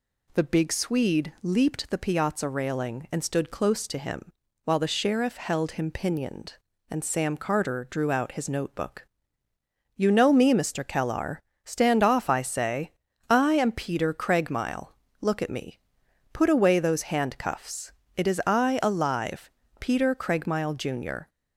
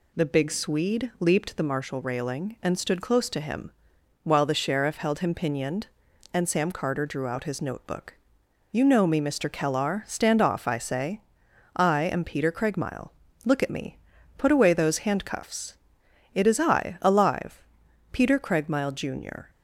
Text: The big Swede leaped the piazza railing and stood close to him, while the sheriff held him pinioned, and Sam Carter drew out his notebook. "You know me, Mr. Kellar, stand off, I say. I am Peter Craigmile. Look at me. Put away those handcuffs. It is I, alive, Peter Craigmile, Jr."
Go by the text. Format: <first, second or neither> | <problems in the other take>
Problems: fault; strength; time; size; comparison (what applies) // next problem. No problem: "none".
first | says "marshal" for "piazza"; at 1.6 s